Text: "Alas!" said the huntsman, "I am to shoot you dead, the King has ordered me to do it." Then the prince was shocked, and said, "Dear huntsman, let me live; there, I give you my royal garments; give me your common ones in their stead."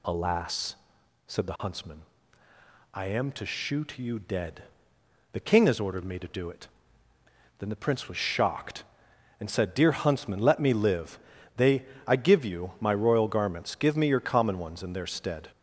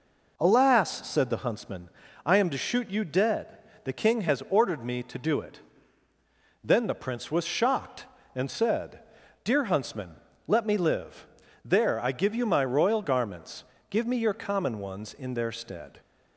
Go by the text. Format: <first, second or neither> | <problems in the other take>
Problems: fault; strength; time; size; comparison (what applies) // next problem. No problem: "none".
second | says "they" for "there"; at 11.5 s